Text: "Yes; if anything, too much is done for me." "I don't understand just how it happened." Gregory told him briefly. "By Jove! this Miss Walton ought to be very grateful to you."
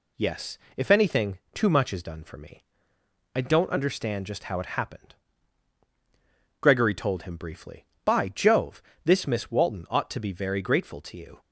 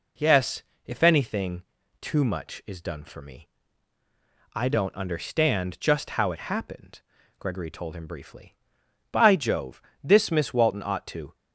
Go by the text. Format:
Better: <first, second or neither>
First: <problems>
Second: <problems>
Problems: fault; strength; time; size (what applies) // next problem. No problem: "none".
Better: first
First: none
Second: stops before "be very grateful to you"; at 11.3 s